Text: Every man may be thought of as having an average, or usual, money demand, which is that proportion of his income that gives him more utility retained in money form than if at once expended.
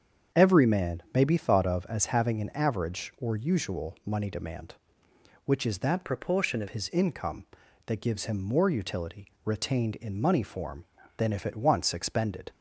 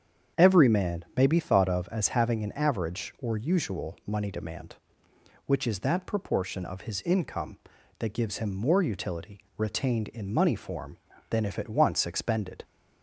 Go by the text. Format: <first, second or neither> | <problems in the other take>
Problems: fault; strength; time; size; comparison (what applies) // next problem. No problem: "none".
second | starts louder than the rest; strong; until 1.4 s; 7.5 dB; strong in the second // changes voice from "proportion" to "of"; from 6.0 to 6.6 s; 0.6 s long // pauses between "utility" and "retained"; slight; at 9.2 s; 0.16 s long; slight in the second